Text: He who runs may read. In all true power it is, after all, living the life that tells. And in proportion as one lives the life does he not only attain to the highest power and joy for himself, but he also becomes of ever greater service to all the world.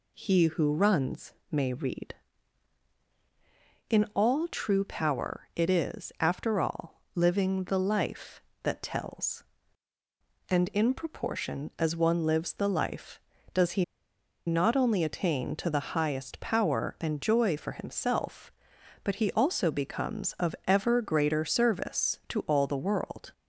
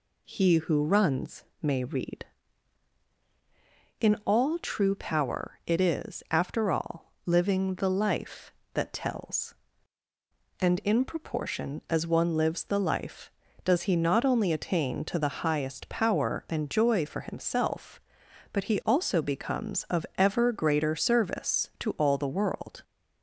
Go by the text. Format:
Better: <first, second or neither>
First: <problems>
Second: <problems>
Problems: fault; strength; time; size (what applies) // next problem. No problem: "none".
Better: second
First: pauses between "runs" and "may"; slight; at 1.3 s; 0.18 s long // pauses between "he" and "not"; noticeable; at 13.8 s; 0.62 s long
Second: pauses between "runs" and "may"; slight; at 1.4 s; 0.18 s long